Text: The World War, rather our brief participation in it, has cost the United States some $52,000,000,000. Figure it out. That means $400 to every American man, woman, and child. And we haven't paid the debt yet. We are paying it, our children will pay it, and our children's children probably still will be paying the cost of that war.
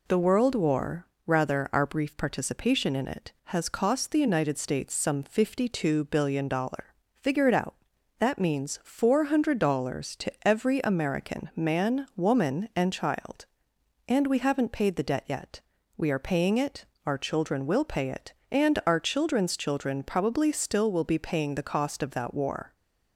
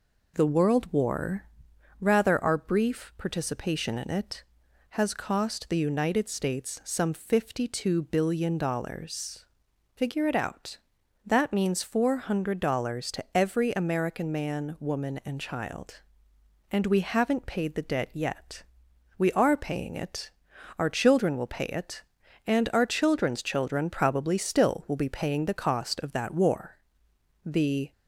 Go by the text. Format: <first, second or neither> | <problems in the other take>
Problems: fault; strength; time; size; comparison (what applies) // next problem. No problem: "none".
first | goes on to say "The"; slight; from 27.4 s on; 0.46 s long